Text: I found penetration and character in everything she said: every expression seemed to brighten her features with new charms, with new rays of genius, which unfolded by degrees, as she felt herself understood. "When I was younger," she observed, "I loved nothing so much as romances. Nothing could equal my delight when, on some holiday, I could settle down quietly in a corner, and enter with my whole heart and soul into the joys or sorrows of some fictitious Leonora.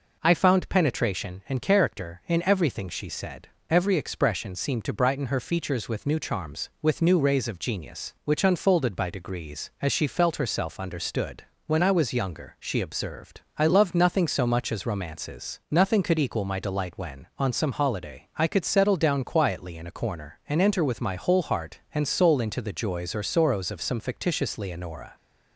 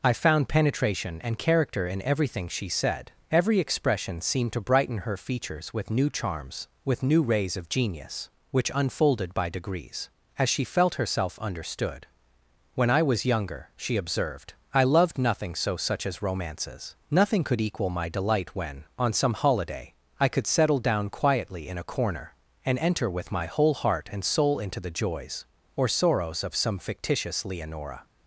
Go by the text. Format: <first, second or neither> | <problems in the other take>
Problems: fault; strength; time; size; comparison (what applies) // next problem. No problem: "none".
first | says "such" for "much"; at 15.7 s